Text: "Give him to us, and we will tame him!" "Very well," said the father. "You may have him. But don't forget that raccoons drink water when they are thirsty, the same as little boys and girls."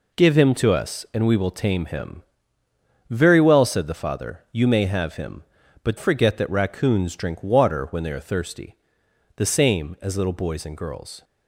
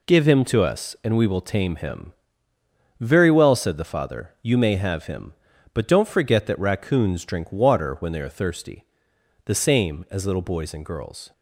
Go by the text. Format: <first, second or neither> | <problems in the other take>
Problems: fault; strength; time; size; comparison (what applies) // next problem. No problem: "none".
second | skips "don't"; at 5.9 s